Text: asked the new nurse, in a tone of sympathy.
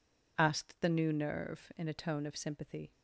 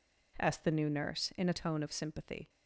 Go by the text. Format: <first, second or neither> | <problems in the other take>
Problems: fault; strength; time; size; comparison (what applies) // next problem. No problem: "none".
second | says "nerve" for "nurse"; at 1.1 s